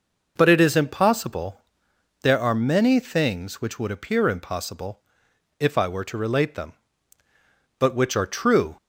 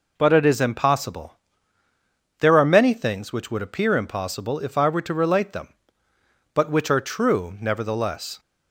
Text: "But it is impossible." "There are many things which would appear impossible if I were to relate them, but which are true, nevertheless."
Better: second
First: pauses between "impossible" and "if"; noticeable; at 5.0 s; 0.58 s long // stops before "nevertheless"; at 8.7 s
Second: none

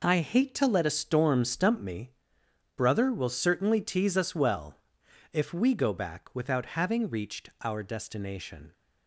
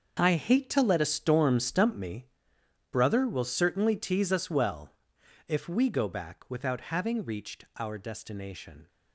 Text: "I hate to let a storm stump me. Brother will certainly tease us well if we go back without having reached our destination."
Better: first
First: pauses between "well" and "if"; noticeable; at 4.7 s; 0.56 s long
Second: gets quieter; strong; throughout; 13 dB // pauses between "well" and "if"; noticeable; at 4.8 s; 0.56 s long

